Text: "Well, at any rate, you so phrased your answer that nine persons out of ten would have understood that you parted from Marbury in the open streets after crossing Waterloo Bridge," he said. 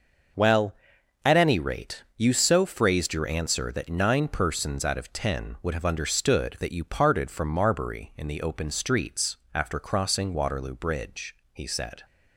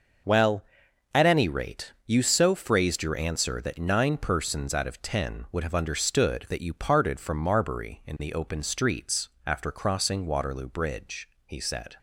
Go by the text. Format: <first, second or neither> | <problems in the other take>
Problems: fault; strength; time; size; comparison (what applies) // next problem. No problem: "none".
neither | pauses between "streets" and "after"; slight; the same in both